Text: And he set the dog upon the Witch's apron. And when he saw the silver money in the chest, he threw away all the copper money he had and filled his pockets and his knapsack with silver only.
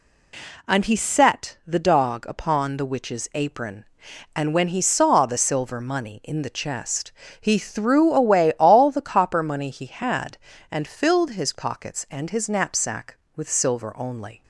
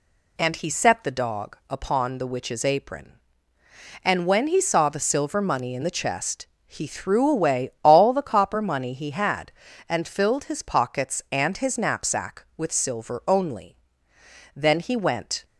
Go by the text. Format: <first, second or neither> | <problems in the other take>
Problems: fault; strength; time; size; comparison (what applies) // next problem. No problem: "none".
first | goes on to say "Then he went"; noticeable; from 14.5 s on; 0.88 s long